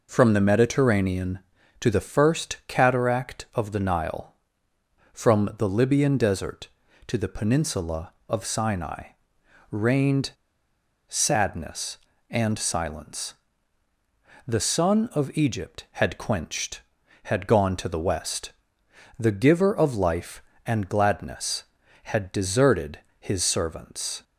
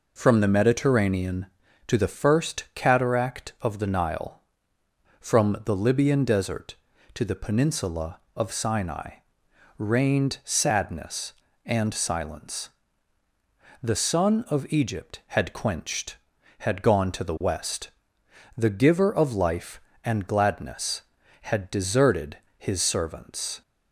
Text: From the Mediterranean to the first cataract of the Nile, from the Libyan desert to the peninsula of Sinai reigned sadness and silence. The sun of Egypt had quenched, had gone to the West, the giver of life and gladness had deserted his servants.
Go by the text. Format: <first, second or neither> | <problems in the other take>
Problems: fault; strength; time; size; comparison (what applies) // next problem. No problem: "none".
second | pauses between "Sinai" and "reigned"; noticeable; at 9.0 s; 0.60 s long; noticeable in the second // pauses between "reigned" and "sadness"; noticeable; at 10.3 s; 0.76 s long // pauses between "deserted" and "his"; slight; at 22.9 s; 0.22 s long; slight in the second